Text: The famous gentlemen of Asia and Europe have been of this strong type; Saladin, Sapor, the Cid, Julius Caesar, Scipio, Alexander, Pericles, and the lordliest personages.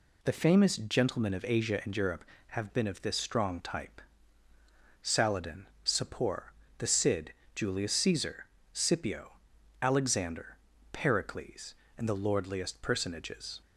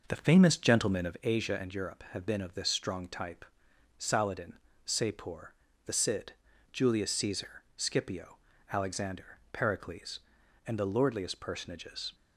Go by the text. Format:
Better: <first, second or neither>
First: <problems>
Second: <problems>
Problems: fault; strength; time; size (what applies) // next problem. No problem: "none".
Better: first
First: none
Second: starts louder than the rest; noticeable; until 1.2 s; 5.5 dB